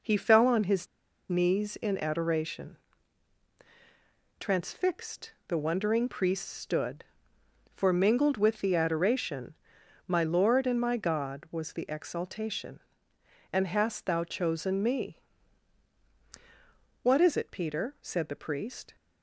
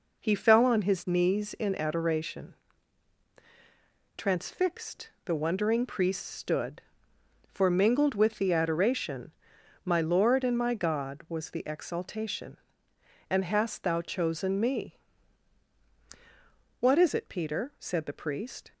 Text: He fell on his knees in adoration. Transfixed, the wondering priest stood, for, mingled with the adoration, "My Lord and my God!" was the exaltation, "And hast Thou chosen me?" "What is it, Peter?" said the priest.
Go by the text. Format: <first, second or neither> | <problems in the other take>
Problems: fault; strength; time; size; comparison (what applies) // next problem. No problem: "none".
second | pauses between "his" and "knees"; at 0.8 s; 0.42 s long